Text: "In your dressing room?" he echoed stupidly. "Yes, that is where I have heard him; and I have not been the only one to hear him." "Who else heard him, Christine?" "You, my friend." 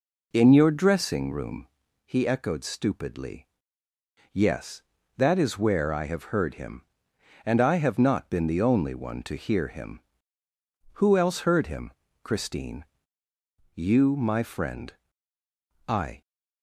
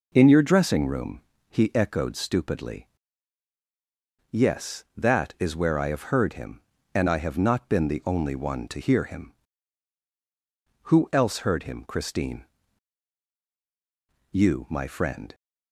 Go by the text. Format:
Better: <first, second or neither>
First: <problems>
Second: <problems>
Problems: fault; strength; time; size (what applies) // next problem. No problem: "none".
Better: second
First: goes on to say "I"; slight; from 15.8 s on; 0.34 s long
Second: none